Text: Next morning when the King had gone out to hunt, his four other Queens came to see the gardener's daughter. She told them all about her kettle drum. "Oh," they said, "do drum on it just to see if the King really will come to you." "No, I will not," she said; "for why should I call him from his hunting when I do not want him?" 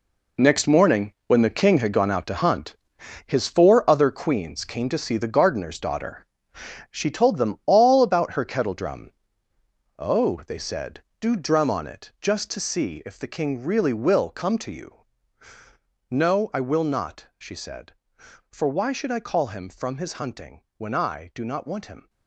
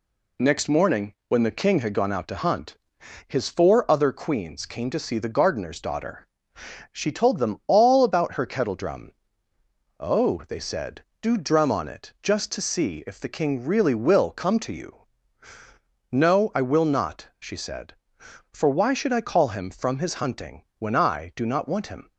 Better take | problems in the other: second | gets quieter; strong; throughout; 11 dB

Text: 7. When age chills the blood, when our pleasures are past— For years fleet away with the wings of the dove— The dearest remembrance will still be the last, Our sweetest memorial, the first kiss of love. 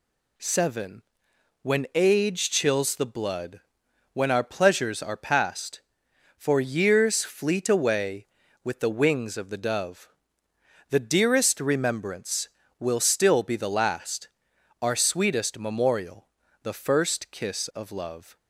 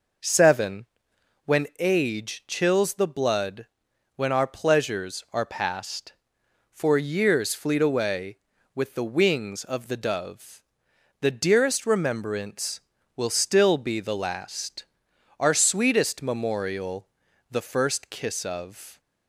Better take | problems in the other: first | stops before "love"; at 18.9 s

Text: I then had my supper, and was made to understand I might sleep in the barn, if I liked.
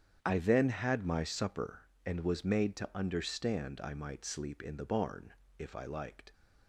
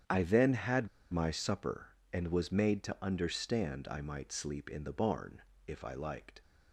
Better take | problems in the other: first | starts louder than the rest; strong; until 1.3 s; 8.5 dB; strong in the first // pauses between "had" and "my"; slight; at 0.8 s; 0.25 s long

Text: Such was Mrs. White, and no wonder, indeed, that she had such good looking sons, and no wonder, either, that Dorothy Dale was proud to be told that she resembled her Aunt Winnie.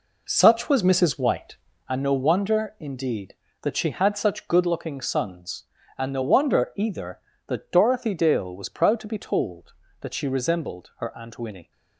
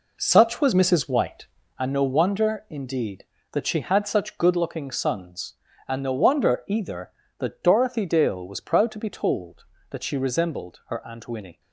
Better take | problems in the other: neither | none

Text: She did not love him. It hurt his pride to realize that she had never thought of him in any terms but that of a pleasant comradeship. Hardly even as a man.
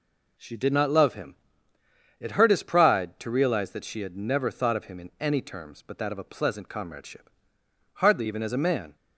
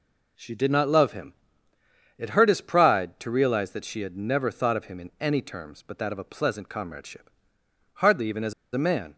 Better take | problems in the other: first | pauses between "as" and "a"; slight; at 8.5 s; 0.20 s long

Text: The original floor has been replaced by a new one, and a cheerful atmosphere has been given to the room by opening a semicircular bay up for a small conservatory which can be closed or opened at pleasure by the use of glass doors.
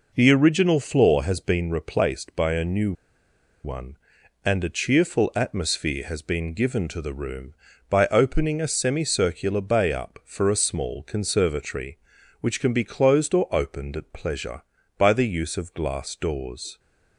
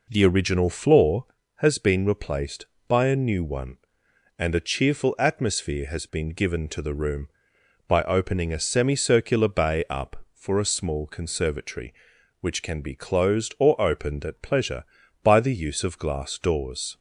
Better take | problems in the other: second | pauses between "new" and "one"; noticeable; at 2.9 s; 0.71 s long

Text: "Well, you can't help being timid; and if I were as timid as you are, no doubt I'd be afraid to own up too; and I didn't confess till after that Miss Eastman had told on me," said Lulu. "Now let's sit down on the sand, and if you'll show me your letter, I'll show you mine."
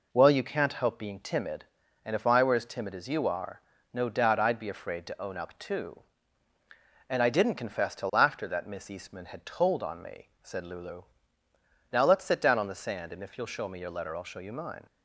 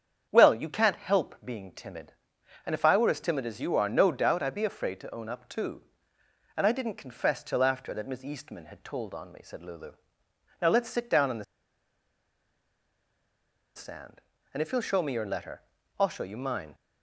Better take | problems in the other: first | starts louder than the rest; strong; until 1.3 s; 8 dB // pauses between "the" and "sand"; strong; at 11.4 s; 2.3 s long

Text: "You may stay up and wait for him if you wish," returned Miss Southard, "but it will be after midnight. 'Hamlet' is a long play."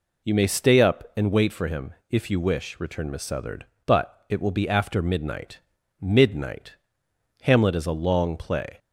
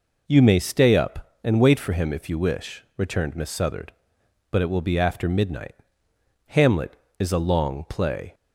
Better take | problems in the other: second | pauses between "him" and "if"; slight; at 1.9 s; 0.18 s long // says "midnight" twice; at 6.0 s

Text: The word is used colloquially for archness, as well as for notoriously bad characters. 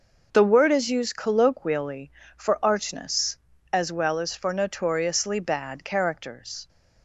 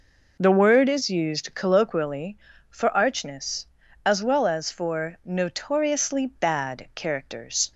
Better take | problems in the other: neither | none

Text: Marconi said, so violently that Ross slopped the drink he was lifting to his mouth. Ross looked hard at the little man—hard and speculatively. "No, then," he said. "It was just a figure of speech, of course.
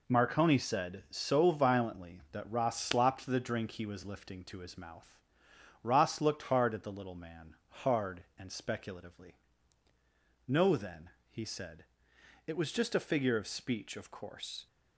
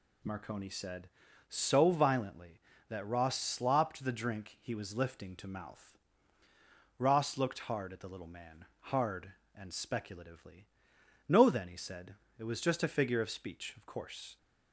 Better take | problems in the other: first | skips "his"; at 5.4 s

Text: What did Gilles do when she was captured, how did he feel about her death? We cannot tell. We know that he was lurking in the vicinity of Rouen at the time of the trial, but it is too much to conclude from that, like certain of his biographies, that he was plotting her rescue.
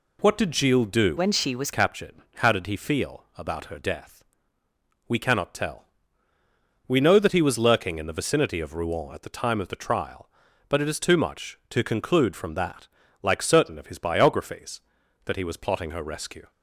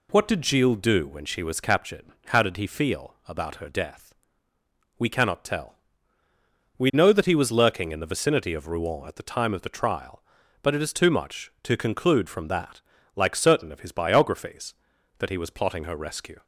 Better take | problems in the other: second | changes voice from "when" to "was"; from 1.1 to 1.7 s; 0.6 s long

